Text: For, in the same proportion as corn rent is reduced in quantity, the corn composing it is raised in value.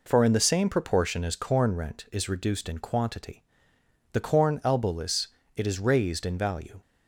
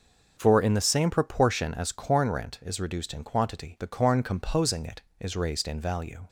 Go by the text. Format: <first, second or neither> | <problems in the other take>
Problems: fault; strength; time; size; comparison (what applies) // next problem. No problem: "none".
second | says "elbowless" for "composing"; at 4.6 s